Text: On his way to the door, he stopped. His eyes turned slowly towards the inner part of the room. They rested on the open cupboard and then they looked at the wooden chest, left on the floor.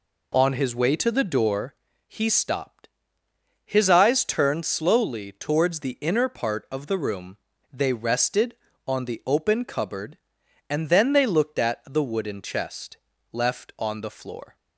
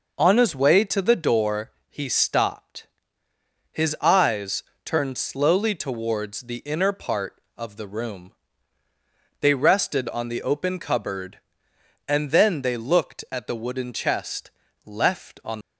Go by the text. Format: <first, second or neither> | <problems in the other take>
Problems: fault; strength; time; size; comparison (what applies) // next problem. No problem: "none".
first | pauses between "eyes" and "turned"; slight; at 4.6 s; 0.22 s long // stops before "the floor"; at 15.6 s